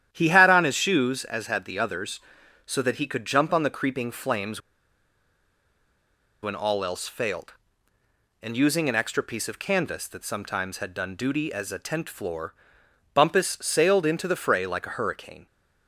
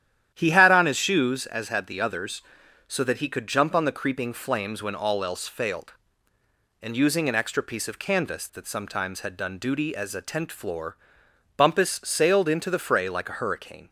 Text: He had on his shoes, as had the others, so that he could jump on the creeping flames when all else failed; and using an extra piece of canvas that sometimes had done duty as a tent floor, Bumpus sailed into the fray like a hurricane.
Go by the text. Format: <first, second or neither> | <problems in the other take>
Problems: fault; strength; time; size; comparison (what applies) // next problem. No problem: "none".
second | starts louder than the rest; strong; until 1.1 s; 10.5 dB; strong in the second // pauses between "flames" and "when"; strong; at 4.5 s; 1.8 s long